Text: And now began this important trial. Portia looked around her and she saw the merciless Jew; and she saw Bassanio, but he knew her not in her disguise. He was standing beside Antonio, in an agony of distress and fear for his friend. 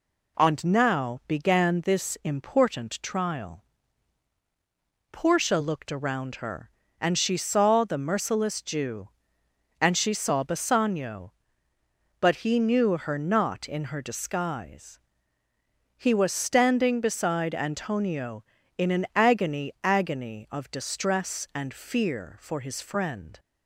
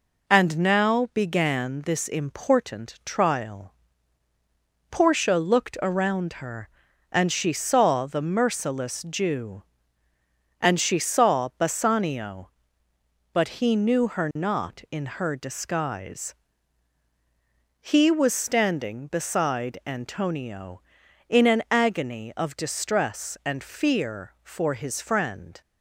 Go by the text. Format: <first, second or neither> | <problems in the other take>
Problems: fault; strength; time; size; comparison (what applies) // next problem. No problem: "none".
second | says "agony" twice; at 19.8 s